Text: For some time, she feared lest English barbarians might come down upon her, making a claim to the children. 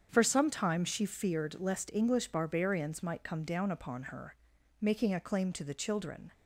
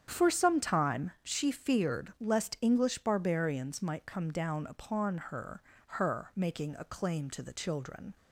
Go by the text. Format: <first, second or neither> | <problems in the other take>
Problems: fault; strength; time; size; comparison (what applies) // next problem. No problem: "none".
first | starts louder than the rest; strong; until 1.0 s; 8.5 dB; strong in the first // says "her" twice; at 5.8 s